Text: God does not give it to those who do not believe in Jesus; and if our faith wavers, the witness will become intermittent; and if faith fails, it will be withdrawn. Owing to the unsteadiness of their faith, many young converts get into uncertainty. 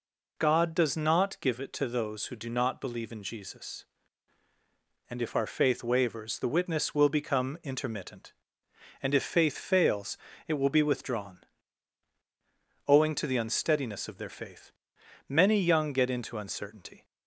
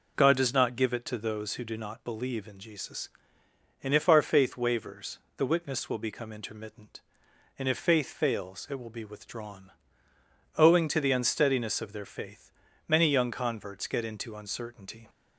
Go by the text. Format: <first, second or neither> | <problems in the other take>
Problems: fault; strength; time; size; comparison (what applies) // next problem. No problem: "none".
second | skips "converts"; at 15.9 s